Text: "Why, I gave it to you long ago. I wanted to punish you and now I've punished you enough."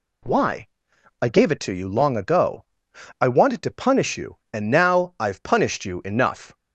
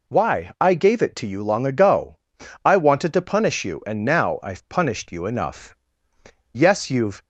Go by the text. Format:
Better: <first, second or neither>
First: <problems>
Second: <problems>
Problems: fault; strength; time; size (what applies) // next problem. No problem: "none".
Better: first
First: none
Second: goes on to say "Yes you've"; noticeable; from 6.5 s on; 0.70 s long